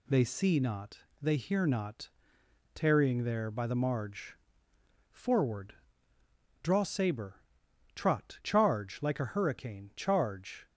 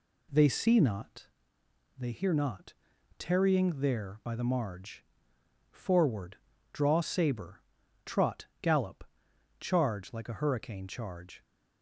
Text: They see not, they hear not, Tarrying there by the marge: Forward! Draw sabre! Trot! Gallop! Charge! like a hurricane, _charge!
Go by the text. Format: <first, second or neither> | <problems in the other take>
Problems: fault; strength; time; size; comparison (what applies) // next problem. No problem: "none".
second | skips "Gallop"; at 8.4 s